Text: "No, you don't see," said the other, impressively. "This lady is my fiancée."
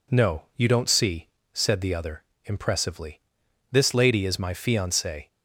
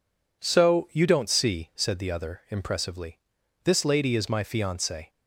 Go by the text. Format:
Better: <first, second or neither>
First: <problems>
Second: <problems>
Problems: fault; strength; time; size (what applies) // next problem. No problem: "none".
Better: first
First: none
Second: says "So" for "No"; at 0.4 s